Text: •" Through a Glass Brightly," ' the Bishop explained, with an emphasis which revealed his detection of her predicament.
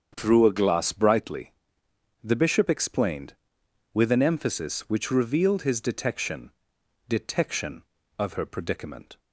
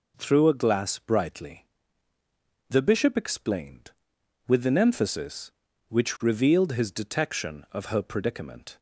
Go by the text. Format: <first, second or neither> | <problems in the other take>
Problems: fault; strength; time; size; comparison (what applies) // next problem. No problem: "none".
second | starts louder than the rest; until 1.1 s; 7 dB // says "detection" twice; at 7.0 s